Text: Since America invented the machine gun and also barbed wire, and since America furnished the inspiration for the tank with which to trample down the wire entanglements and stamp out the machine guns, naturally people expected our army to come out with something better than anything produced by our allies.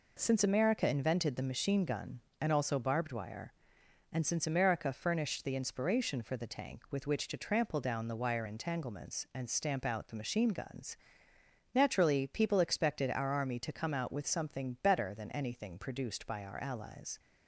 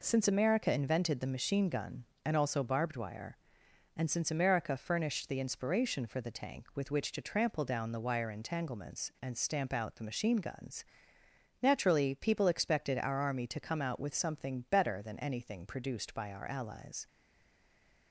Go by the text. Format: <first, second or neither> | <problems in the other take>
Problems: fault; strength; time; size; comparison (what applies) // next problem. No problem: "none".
first | stays silent after the last word; from 17.0 s on; 1.1 s long